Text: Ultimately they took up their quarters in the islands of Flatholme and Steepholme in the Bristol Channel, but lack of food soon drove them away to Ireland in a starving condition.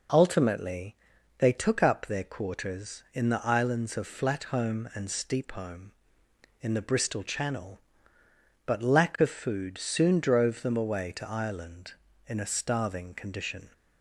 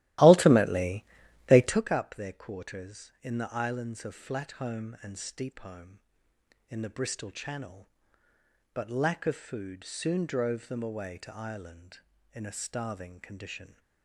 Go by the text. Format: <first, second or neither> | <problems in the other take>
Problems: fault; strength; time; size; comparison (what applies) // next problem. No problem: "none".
first | starts louder than the rest; strong; until 1.9 s; 15.5 dB // pauses between "Ultimately" and "they"; at 1.0 s; 0.44 s long; also in the first